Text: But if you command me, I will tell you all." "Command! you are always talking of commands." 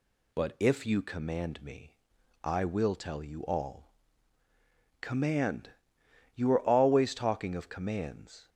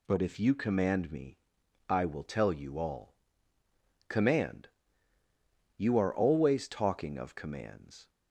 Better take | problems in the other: neither | none

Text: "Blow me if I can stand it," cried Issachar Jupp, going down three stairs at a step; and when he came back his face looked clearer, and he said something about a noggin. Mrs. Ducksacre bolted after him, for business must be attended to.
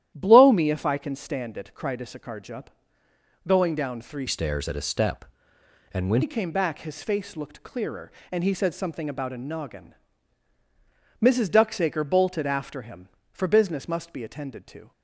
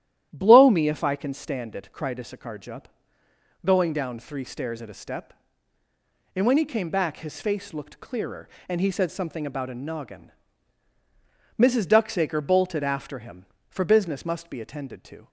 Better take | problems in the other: second | starts louder than the rest; strong; until 1.1 s; 11.5 dB; strong in the second // changes voice from "stairs" to "when"; from 4.2 to 6.2 s; 2.0 s long

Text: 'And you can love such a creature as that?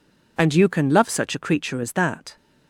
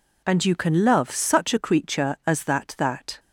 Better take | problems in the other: first | says "that" twice; at 2.7 s

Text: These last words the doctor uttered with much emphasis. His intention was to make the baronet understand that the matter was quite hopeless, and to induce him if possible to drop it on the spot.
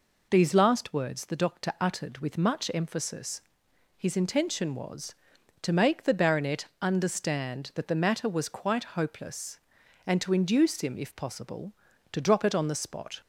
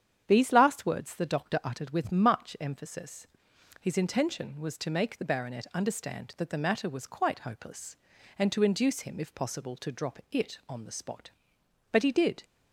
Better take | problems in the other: first | starts louder than the rest; strong; until 1.2 s; 9 dB // goes on to say "But he did"; from 11.9 s on; 0.52 s long

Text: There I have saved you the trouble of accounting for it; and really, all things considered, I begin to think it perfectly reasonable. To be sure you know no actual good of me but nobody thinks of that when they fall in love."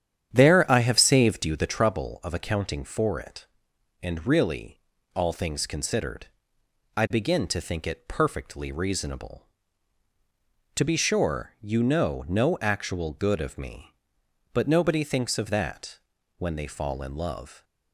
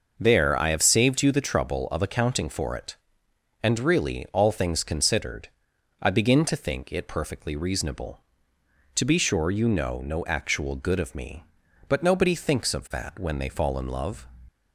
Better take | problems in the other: second | starts louder than the rest; strong; until 1.7 s; 9 dB // pauses between "that" and "when"; at 15.9 s; 0.38 s long

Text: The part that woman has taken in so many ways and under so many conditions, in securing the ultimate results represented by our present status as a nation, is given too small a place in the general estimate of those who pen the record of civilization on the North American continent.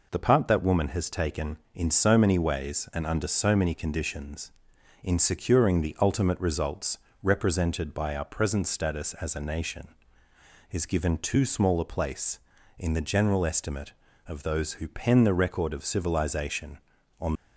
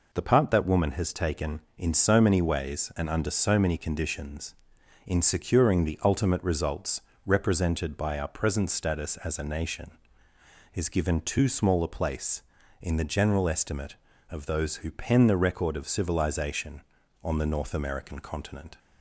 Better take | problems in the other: second | pauses between "results" and "represented"; slight; at 6.9 s; 0.26 s long; slight in the second // stops before "the North American continent"; at 17.3 s

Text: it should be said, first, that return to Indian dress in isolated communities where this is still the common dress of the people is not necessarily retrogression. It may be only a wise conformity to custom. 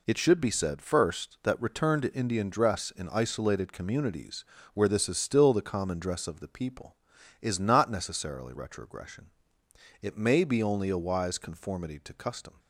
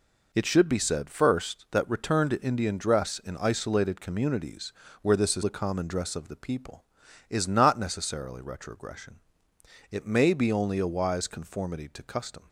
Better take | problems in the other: first | pauses between "communities" and "where"; slight; at 4.7 s; 0.30 s long; slight in the first // skips "still"; at 5.4 s

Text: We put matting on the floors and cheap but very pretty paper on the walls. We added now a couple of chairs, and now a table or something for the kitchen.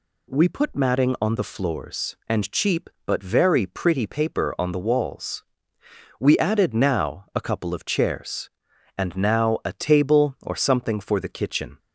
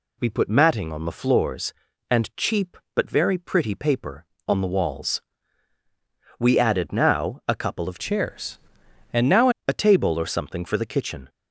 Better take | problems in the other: first | changes voice from "chairs" to "now"; from 7.9 to 9.4 s; 1.5 s long

